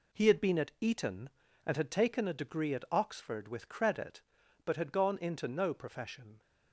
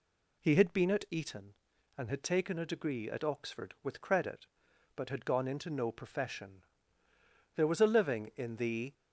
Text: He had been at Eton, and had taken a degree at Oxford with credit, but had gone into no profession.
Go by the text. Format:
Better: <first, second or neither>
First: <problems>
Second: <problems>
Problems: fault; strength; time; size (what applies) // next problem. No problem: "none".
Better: first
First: none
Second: goes on to say "There was a living in the"; from 7.5 s on; 1.3 s long